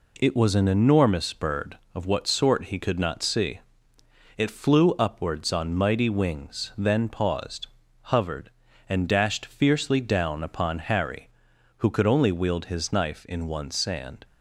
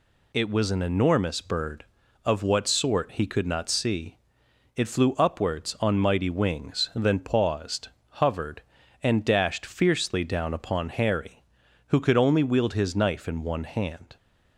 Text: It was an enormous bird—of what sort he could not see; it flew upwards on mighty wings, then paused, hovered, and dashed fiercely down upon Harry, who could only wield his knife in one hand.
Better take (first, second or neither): second